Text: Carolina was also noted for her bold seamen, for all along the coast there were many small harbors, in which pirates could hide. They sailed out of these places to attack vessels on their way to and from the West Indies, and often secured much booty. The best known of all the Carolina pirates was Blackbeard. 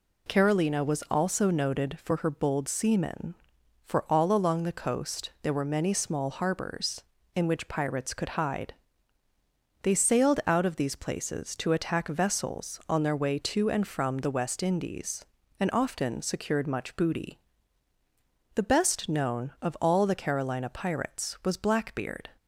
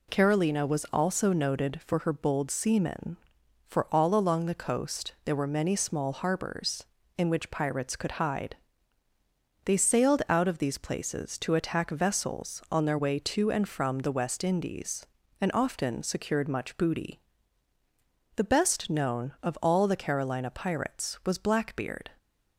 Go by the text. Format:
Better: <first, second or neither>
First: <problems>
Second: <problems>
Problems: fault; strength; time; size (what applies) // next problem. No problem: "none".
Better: neither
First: none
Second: none